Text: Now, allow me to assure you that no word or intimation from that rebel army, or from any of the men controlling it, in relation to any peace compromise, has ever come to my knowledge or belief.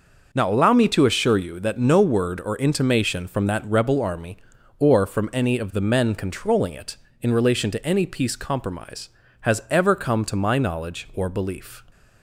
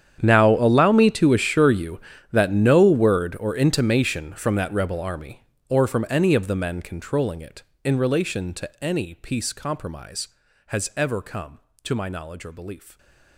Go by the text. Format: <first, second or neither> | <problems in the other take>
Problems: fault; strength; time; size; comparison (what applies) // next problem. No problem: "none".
first | gets quieter; strong; throughout; 20.5 dB